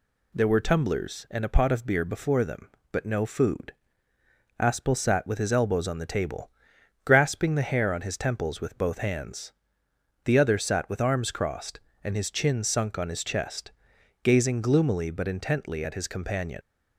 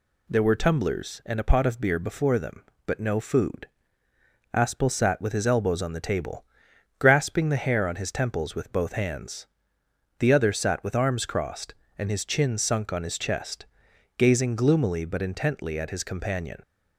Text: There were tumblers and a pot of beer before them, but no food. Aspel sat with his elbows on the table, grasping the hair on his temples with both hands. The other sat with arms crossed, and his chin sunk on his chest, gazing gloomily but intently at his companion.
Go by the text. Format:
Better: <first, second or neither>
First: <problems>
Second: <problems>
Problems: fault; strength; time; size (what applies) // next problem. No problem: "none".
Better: second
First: leaves "companion" unfinished; at 16.6 s; 45 ms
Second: none